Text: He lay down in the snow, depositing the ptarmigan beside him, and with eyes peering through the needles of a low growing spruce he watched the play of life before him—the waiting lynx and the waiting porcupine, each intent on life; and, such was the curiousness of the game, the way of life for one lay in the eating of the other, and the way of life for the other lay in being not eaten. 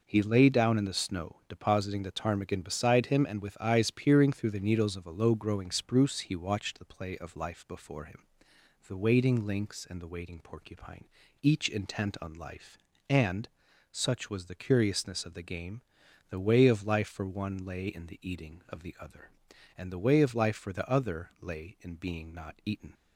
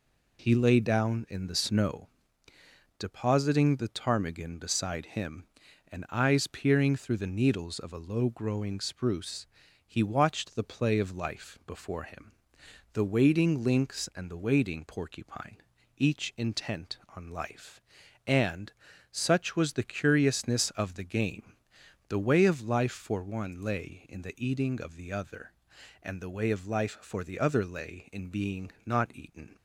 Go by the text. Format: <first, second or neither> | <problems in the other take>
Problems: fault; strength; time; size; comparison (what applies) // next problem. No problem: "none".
first | skips "with"; at 6.0 s // pauses between "spruce" and "he"; at 9.4 s; 0.40 s long